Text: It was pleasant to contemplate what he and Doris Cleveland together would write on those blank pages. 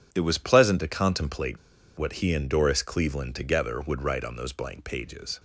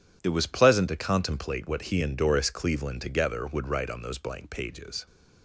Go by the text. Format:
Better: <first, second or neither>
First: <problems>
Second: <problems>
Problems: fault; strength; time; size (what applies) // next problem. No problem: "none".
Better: second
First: pauses between "contemplate" and "what"; at 1.5 s; 0.40 s long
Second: none